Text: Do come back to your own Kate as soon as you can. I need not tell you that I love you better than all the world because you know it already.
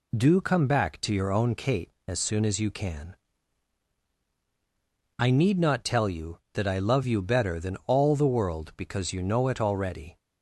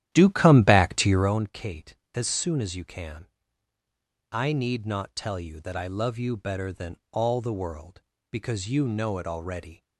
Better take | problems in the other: first | starts louder than the rest; strong; until 1.4 s; 12 dB // pauses between "than" and "all"; slight; at 6.9 s; 0.16 s long

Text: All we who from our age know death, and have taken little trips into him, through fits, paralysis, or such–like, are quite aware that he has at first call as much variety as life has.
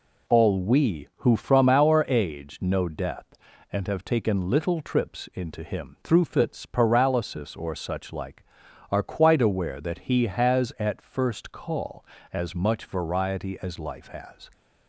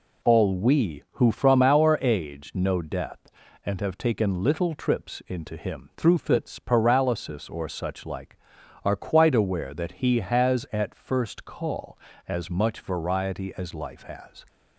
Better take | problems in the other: neither | none

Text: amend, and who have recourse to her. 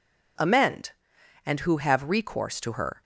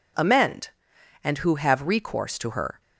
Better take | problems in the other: neither | none

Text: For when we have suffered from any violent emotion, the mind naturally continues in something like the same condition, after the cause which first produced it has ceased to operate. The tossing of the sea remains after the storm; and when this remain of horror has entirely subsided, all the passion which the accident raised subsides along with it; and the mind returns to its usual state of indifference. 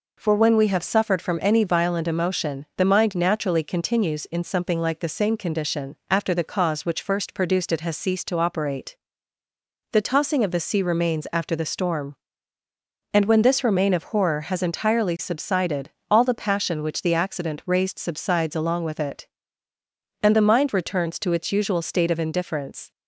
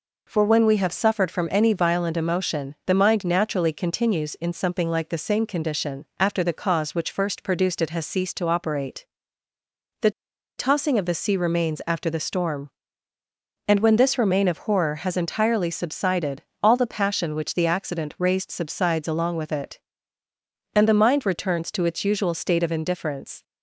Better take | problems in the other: first | pauses between "The" and "tossing"; noticeable; at 10.0 s; 0.48 s long

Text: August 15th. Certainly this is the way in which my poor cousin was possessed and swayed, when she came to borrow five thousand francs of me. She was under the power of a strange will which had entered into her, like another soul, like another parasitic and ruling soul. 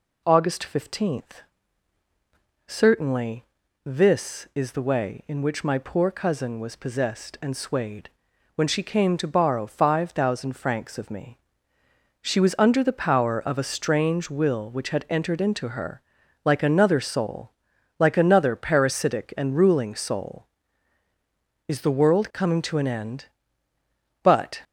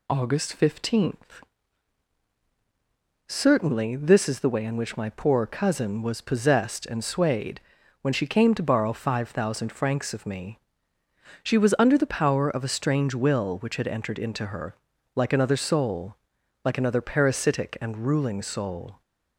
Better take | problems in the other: second | pauses between "Certainly" and "this"; at 3.4 s; 0.42 s long // goes on to say "Is the world coming to an end But"; strong; from 21.6 s on; 2.9 s long

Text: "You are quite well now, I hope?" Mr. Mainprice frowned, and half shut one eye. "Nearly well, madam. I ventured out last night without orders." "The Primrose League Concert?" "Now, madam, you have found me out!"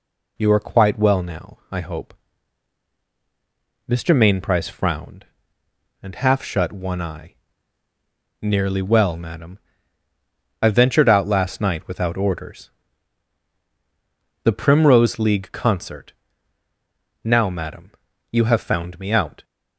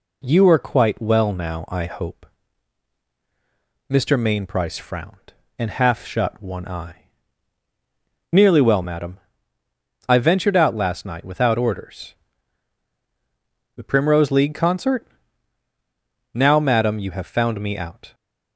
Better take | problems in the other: neither | none

